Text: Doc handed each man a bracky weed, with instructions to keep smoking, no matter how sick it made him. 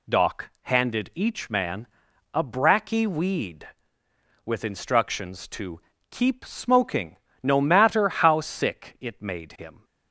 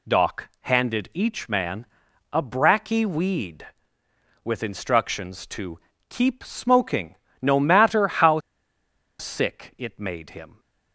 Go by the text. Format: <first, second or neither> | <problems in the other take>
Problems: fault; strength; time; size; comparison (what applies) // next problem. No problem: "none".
first | pauses between "man" and "a"; noticeable; at 1.8 s; 0.48 s long; noticeable in the first // pauses between "to" and "keep"; slight; at 5.7 s; 0.30 s long; slight in the first // pauses between "how" and "sick"; noticeable; at 8.3 s; 0.80 s long